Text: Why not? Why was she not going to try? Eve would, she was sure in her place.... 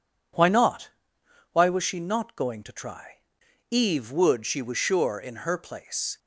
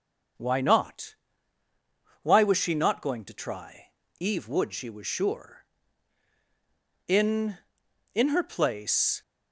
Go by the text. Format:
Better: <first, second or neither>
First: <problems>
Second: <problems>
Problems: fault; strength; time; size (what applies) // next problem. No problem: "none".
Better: first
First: none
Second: starts louder than the rest; until 2.4 s; 6 dB // says "in" twice; at 8.1 s